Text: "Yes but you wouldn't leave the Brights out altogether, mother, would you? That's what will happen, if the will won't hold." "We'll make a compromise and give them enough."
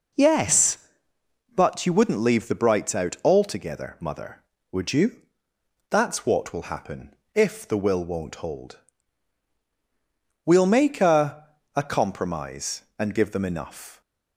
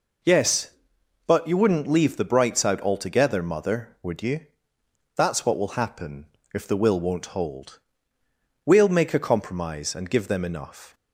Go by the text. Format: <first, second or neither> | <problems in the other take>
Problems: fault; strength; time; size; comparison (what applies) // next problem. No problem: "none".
second | says "a" twice; at 11.7 s